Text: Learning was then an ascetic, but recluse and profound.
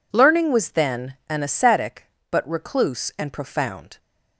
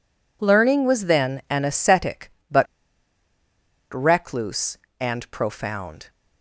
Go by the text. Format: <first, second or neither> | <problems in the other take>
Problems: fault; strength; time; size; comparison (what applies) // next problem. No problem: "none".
first | pauses between "but" and "recluse"; strong; at 2.6 s; 1.2 s long